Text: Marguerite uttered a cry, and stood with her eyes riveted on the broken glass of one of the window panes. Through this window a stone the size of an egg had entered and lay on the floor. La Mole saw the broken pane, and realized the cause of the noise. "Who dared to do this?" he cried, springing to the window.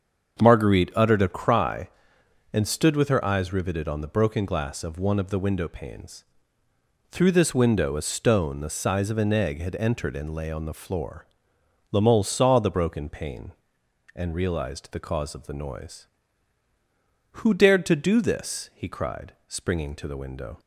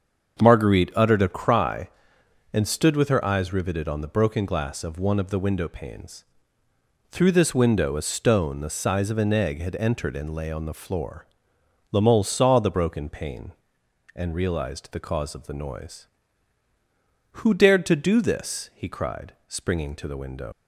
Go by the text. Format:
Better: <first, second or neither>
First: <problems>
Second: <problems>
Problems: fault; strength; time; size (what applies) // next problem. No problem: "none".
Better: first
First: starts louder than the rest; until 1.4 s; 7 dB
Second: starts louder than the rest; until 1.4 s; 7 dB // leaves "window" unfinished; at 20.5 s; 75 ms